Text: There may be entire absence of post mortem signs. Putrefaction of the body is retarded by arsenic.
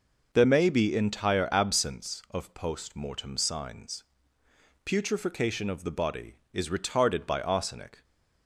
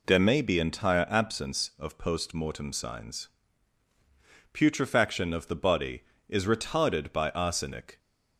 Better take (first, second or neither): neither